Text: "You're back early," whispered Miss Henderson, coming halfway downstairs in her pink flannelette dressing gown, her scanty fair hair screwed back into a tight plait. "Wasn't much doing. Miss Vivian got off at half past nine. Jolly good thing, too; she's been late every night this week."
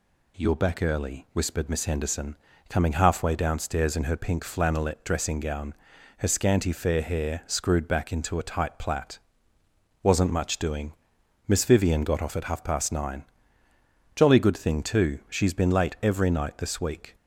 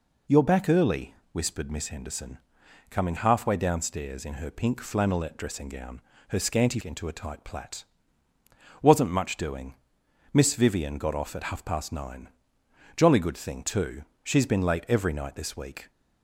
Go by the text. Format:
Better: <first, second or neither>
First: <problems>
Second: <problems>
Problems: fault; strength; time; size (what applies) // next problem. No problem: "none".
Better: first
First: none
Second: skips "fair hair screwed back"; at 6.8 s